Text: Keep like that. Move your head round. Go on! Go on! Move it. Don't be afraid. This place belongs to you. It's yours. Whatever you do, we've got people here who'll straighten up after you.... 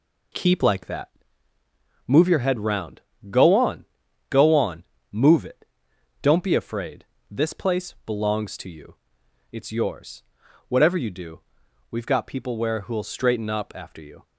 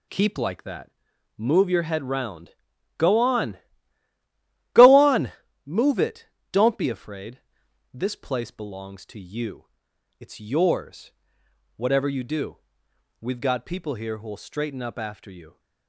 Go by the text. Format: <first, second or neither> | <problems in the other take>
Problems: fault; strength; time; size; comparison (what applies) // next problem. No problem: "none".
second | says "where" for "here"; at 12.5 s